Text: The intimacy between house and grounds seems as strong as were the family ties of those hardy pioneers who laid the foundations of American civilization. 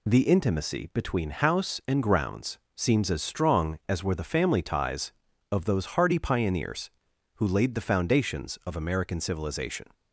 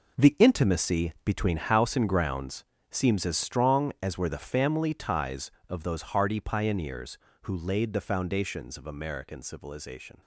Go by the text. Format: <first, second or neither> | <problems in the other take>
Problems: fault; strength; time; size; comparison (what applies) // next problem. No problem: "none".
first | gets quieter; strong; throughout; 11.5 dB // pauses between "grounds" and "seems"; slight; at 2.6 s; 0.26 s long; slight in the first